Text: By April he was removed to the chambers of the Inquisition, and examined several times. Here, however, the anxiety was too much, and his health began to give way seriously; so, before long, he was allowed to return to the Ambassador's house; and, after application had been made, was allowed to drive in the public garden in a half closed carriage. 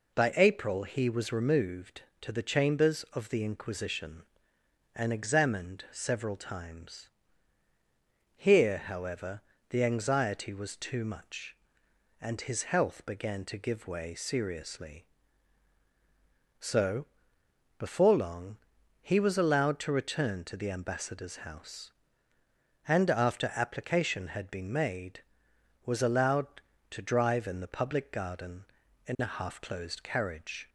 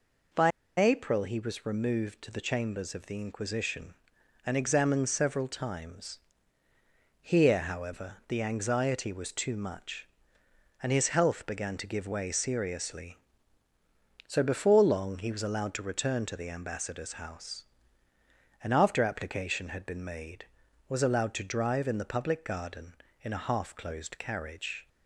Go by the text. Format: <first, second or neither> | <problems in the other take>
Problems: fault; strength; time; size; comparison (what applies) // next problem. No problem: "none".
first | pauses between "By" and "April"; slight; at 0.5 s; 0.29 s long